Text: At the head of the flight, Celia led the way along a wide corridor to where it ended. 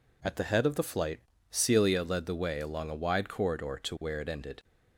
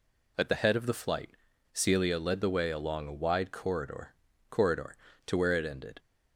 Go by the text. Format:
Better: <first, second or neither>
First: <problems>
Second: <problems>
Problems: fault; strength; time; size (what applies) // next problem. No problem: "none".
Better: first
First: none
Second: says "corridor" twice; at 4.5 s